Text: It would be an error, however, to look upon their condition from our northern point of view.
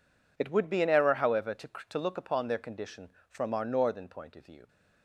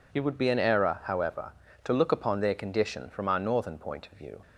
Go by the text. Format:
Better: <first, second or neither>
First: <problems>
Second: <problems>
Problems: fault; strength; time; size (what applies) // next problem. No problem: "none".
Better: second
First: says "to" twice; at 1.8 s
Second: none